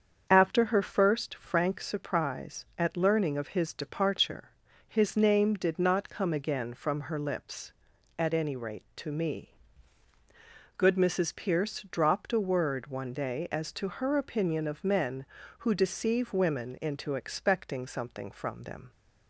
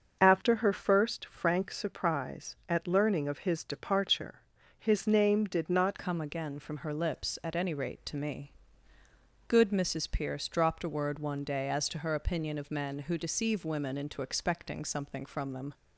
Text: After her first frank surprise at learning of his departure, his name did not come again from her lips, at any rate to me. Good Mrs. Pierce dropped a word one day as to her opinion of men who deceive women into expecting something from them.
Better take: first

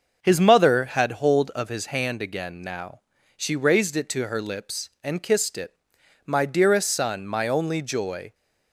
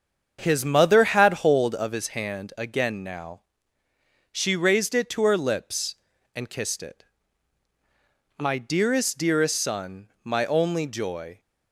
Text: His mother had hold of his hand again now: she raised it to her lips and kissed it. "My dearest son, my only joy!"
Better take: first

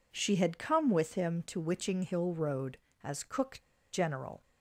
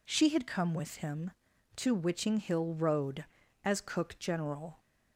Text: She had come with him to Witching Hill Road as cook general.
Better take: second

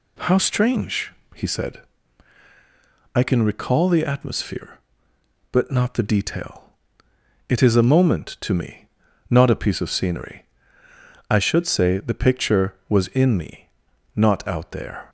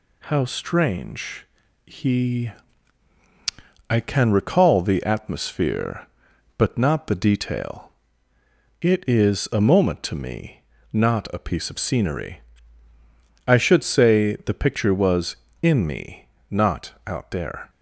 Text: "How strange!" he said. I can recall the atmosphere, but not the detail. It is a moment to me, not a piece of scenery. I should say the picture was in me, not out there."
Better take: first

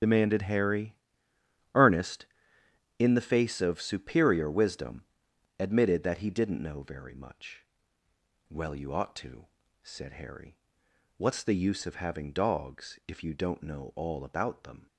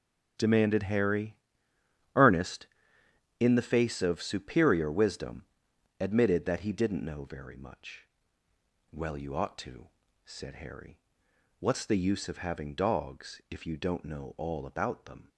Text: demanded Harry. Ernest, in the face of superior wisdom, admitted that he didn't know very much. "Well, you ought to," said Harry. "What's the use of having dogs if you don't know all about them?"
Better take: second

